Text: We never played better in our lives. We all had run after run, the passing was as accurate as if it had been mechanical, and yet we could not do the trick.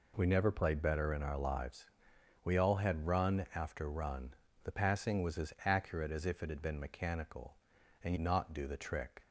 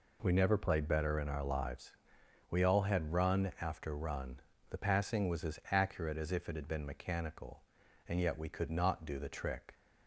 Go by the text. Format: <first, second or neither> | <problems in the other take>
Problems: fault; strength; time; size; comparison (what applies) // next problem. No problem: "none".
second | skips "yet we could"; at 8.1 s